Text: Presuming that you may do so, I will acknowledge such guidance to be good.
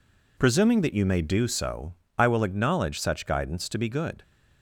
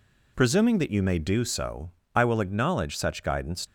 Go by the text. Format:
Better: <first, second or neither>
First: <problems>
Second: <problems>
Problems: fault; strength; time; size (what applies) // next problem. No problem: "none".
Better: first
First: none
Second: stops before "to be good"; at 3.6 s